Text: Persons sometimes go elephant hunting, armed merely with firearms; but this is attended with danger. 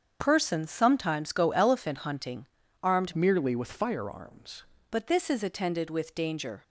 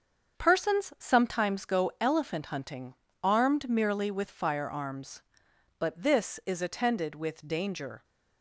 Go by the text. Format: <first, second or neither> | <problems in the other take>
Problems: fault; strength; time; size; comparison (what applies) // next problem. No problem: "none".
second | starts louder than the rest; strong; until 1.2 s; 7.5 dB; also in the second // changes voice from "merely" to "firearms"; from 3.1 to 4.6 s; 1.5 s long